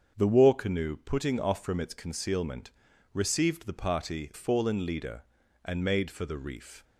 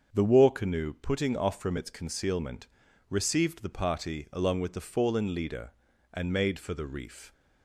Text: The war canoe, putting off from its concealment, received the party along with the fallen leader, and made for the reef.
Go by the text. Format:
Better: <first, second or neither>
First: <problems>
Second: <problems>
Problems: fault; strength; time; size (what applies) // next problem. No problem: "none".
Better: second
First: starts louder than the rest; strong; until 1.1 s; 7 dB // skips "along with the"; at 4.3 s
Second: starts louder than the rest; until 1.1 s; 7 dB